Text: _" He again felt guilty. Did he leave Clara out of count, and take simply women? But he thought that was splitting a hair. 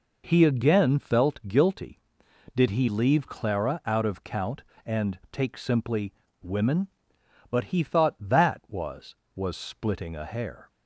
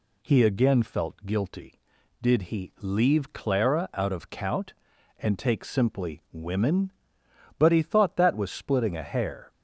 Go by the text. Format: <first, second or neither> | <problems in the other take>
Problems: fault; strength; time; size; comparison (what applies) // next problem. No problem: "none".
second | pauses between "simply" and "women"; slight; at 6.1 s; 0.28 s long // says "was" twice; at 9.3 s